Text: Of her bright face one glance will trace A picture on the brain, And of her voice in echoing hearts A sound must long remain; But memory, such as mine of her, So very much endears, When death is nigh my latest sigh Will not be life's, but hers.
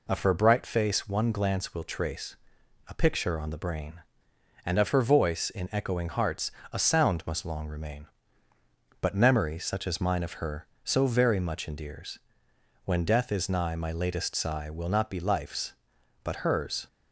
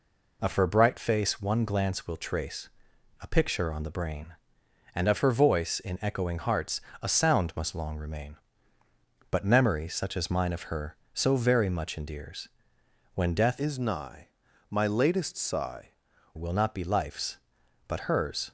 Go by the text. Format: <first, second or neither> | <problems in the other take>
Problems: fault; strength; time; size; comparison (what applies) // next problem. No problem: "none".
first | pauses between "trace" and "A"; noticeable; at 2.6 s; 0.52 s long; noticeable in the first // pauses between "hearts" and "A"; slight; at 6.8 s; 0.22 s long; slight in the first // changes voice from "is" to "sigh"; from 13.5 to 15.8 s; 2.3 s long // pauses between "nigh" and "my"; at 14.2 s; 0.42 s long